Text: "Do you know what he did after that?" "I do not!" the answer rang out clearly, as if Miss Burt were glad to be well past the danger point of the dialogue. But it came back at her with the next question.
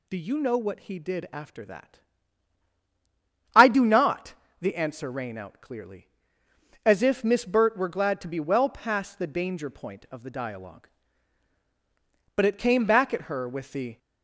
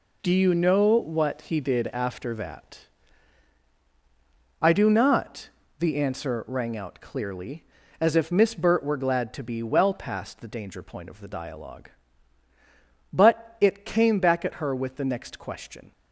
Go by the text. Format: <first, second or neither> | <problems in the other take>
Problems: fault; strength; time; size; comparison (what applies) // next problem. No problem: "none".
second | stops before "next question"; at 13.9 s